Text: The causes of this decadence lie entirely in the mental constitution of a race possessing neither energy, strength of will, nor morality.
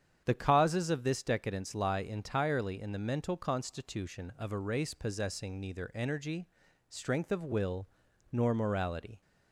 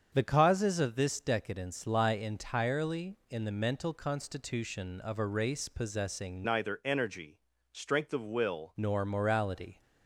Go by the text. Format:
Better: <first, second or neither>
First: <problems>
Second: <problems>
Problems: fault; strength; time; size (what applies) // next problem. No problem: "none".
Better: first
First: starts louder than the rest; strong; until 1.2 s; 8.5 dB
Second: starts louder than the rest; strong; until 1.1 s; 7.5 dB // changes voice from "neither" to "will"; from 6.4 to 8.7 s; 2.3 s long